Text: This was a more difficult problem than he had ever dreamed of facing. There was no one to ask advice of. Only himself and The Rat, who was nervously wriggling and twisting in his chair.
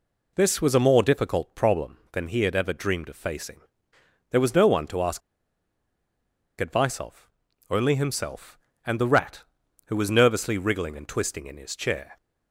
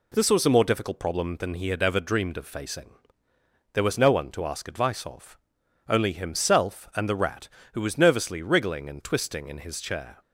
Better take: second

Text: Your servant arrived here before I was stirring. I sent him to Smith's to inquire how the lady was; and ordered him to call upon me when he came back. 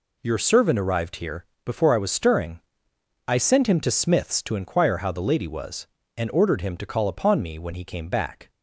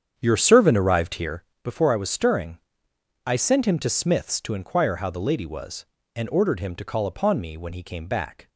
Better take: first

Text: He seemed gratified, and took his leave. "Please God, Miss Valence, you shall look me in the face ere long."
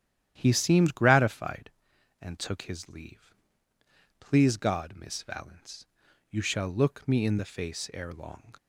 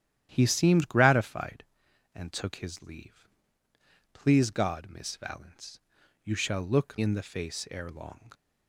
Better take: first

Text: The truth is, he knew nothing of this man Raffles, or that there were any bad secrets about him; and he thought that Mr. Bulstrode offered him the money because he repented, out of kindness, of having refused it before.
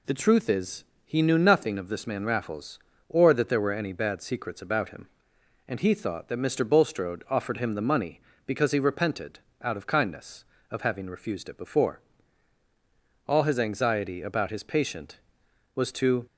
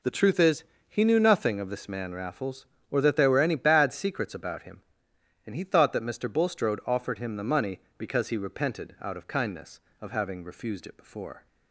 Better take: second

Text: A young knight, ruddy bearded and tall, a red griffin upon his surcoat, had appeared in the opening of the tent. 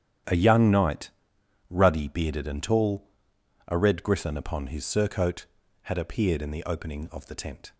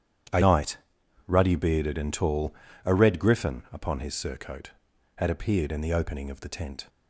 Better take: first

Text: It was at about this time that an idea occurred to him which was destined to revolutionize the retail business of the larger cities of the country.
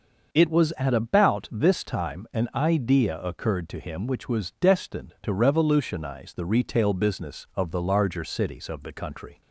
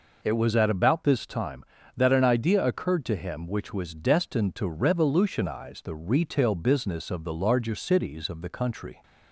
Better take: second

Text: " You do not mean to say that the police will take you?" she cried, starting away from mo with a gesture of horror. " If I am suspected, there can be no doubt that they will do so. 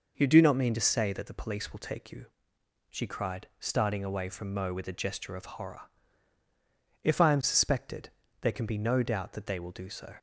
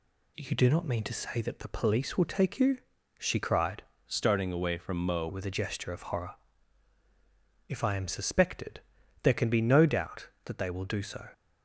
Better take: first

